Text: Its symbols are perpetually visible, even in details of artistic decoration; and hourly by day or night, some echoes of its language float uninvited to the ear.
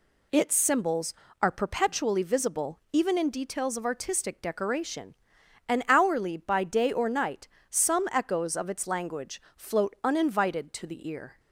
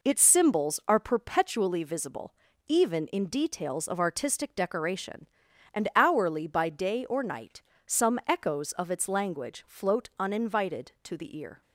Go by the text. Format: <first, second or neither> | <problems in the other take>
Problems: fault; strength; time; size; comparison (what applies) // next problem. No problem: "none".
neither | none